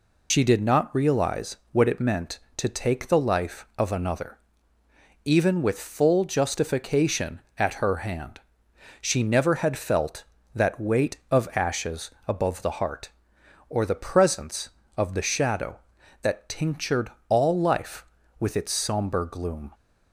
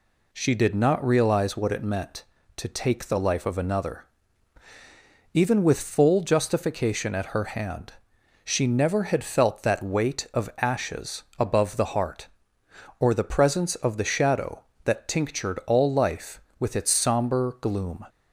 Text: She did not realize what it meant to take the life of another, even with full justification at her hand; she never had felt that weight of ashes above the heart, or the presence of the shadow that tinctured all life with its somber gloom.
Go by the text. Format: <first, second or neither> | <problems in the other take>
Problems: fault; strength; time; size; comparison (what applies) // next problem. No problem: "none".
second | loses the start of "She"; at 0.3 s; 65 ms // pauses between "realize" and "what"; slight; at 1.5 s; 0.16 s long // pauses between "ashes" and "above"; slight; at 12.0 s; 0.16 s long // pauses between "tinctured" and "all"; slight; at 17.1 s; 0.16 s long